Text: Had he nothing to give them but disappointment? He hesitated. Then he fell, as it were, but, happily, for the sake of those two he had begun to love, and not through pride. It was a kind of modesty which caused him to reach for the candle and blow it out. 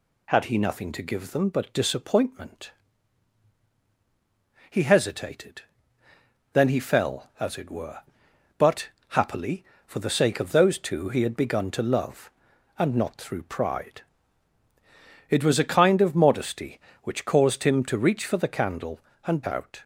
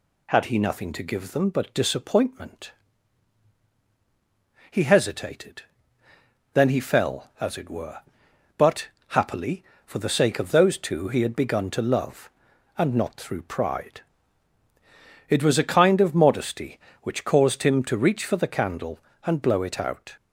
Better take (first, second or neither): second